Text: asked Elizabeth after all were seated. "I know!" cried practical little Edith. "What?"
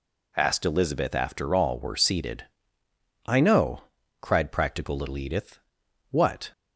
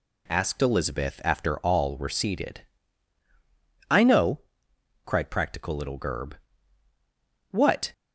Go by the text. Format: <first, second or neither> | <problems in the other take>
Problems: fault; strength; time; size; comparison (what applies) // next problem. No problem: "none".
first | says "Gerb" for "Edith"; at 5.9 s